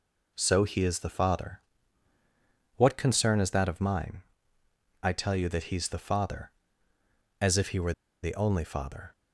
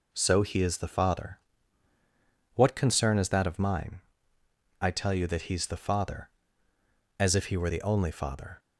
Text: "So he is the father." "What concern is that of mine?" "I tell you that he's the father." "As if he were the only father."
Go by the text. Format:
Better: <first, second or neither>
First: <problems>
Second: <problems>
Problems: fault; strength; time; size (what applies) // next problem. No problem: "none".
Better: second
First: pauses between "were" and "the"; slight; at 7.9 s; 0.29 s long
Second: none